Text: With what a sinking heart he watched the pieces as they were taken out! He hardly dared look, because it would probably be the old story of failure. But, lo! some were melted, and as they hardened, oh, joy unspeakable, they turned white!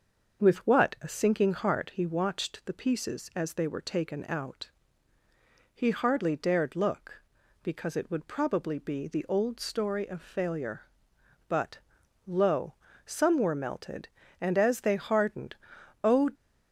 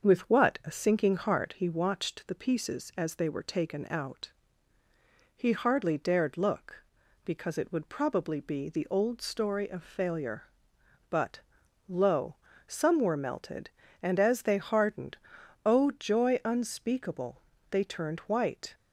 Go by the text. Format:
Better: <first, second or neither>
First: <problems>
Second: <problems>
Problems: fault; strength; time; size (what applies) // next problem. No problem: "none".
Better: second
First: starts louder than the rest; until 1.4 s; 6.5 dB // stops before "joy unspeakable they turned white"; at 16.3 s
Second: starts louder than the rest; until 1.1 s; 6.5 dB